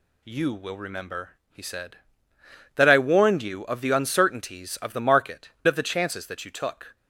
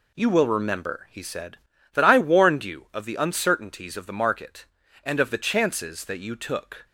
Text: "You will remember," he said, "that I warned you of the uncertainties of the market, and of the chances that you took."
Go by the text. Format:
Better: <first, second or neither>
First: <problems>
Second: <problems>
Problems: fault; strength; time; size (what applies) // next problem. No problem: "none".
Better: second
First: skips "and"; at 5.5 s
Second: none